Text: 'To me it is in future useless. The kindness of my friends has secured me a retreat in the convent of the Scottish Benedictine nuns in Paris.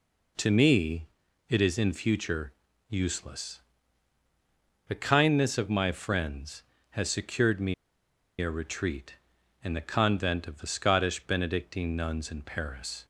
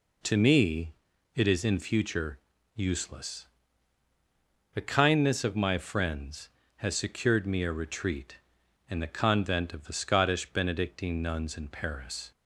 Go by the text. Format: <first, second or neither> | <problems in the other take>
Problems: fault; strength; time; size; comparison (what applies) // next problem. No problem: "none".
second | pauses between "me" and "it"; at 1.0 s; 0.42 s long; also in the second // pauses between "future" and "useless"; slight; at 2.5 s; 0.36 s long; slight in the second // pauses between "me" and "a"; noticeable; at 7.7 s; 0.66 s long